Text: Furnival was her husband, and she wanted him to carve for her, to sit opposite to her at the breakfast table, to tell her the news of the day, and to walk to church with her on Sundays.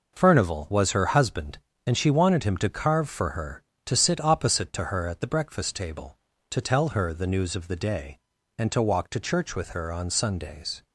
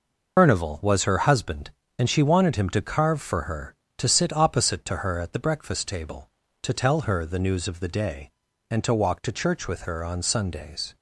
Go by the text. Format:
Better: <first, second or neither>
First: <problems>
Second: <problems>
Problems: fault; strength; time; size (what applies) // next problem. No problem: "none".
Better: first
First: none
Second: loses the start of "Furnival"; at 0.3 s; 105 ms